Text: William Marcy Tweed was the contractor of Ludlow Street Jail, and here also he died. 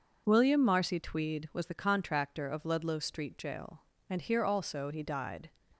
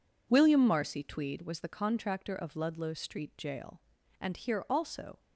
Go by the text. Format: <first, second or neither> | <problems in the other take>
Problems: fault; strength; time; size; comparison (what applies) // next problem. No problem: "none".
first | stops before "he died"; at 5.1 s